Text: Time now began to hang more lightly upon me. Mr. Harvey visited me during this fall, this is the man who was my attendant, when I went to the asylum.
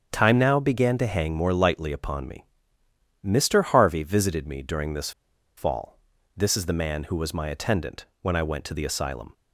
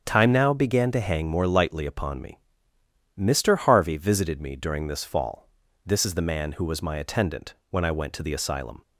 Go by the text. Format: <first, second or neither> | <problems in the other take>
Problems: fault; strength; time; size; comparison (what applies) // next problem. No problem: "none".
second | starts louder than the rest; strong; until 1.1 s; 7.5 dB; strong in the second // pauses between "this" and "fall"; at 5.1 s; 0.45 s long